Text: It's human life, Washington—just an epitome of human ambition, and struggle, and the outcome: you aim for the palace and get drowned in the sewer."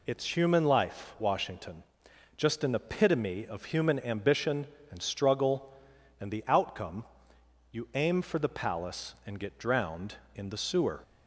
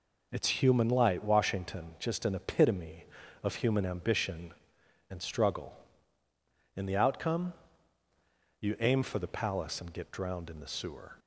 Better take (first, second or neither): first